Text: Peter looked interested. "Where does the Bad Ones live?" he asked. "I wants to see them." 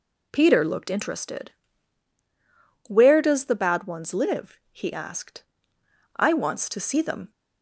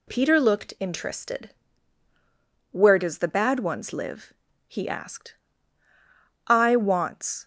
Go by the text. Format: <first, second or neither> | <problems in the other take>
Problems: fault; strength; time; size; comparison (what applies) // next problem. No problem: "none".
first | stops before "to see them"; at 7.4 s